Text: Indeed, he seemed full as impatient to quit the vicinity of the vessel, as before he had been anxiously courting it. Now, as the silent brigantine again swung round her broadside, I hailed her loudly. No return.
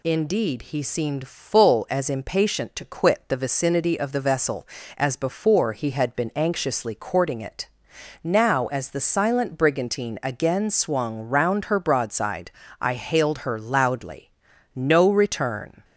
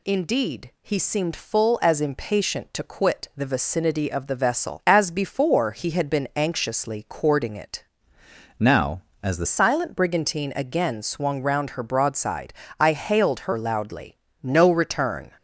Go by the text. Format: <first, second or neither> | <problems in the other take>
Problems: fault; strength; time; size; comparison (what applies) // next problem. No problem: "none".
first | changes voice from "Now" to "the"; from 8.5 to 9.4 s; 0.9 s long